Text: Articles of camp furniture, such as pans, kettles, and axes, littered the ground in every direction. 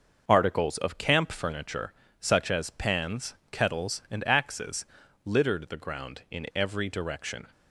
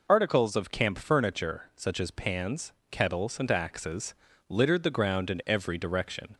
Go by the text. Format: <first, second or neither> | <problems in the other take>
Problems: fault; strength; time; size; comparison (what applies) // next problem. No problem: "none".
second | gets quieter; noticeable; throughout; 5.5 dB